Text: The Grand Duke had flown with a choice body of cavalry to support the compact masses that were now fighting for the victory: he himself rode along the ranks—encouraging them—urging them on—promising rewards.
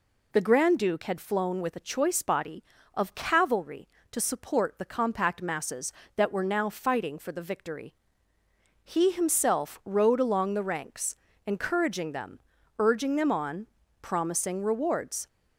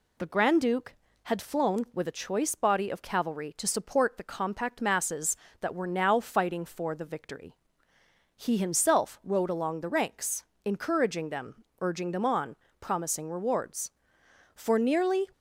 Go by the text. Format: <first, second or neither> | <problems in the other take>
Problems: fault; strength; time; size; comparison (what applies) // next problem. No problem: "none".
first | goes on to say "For nearly"; noticeable; from 14.5 s on; 0.72 s long